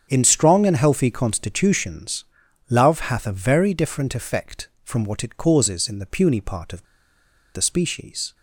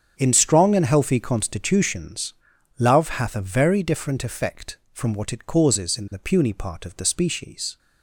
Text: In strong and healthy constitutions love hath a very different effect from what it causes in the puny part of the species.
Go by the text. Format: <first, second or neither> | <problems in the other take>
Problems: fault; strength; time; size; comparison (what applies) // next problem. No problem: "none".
second | starts louder than the rest; strong; until 1.1 s; 8 dB; strong in the second // pauses between "constitutions" and "love"; noticeable; at 2.2 s; 0.46 s long; noticeable in the second // pauses between "of" and "the"; noticeable; at 6.8 s; 0.73 s long